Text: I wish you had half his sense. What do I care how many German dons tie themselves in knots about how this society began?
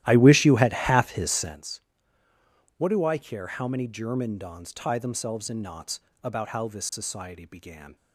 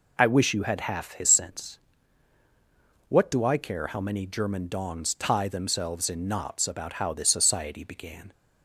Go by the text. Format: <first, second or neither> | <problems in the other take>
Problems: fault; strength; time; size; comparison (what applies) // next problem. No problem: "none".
second | starts louder than the rest; strong; until 1.6 s; 13.5 dB // pauses between "knots" and "about"; slight; at 6.0 s; 0.22 s long